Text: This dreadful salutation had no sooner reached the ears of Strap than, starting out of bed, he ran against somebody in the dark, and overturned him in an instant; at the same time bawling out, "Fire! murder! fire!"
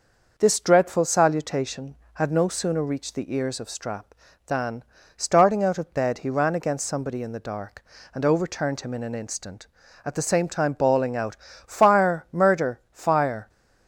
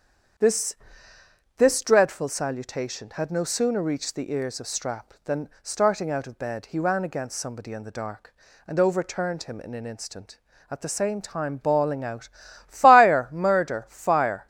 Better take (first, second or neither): first